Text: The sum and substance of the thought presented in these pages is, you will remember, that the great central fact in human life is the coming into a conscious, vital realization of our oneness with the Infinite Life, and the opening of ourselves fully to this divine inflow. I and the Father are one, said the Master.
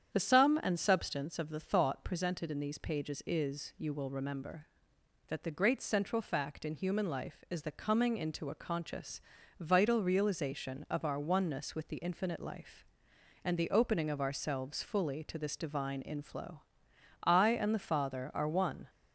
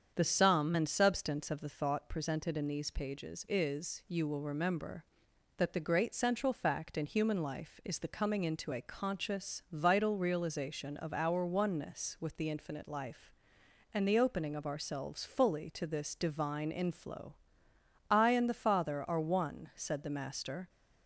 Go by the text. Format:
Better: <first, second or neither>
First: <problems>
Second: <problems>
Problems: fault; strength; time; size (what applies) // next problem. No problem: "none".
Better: second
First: starts louder than the rest; strong; until 1.1 s; 8.5 dB // stops before "said the Master"; at 18.8 s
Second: starts louder than the rest; strong; until 1.1 s; 7.5 dB